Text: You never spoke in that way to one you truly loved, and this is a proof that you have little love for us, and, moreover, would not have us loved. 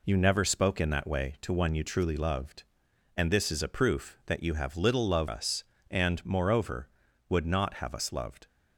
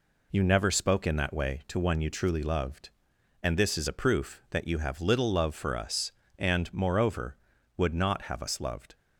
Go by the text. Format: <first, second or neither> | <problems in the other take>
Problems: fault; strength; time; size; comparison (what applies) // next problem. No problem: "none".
second | skips "for"; at 5.2 s